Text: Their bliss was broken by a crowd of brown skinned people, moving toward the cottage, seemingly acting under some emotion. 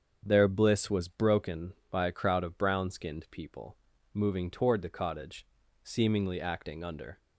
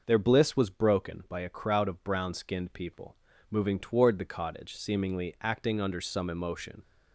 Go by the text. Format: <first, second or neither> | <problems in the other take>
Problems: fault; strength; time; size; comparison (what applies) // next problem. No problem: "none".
second | starts louder than the rest; until 1.2 s; 7 dB // stops before "some emotion"; at 7.1 s